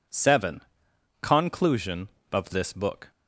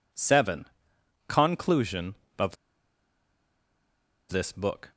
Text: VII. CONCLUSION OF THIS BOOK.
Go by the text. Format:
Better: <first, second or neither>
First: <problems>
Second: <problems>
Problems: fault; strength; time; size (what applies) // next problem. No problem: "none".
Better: first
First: none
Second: pauses between "OF" and "THIS"; strong; at 2.5 s; 1.7 s long